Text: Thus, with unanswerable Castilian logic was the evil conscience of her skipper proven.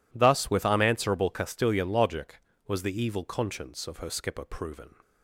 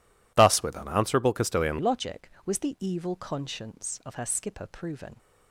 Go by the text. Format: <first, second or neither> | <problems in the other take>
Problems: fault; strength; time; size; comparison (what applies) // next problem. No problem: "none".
first | changes voice at "logic"; from 1.7 s on; 3.4 s long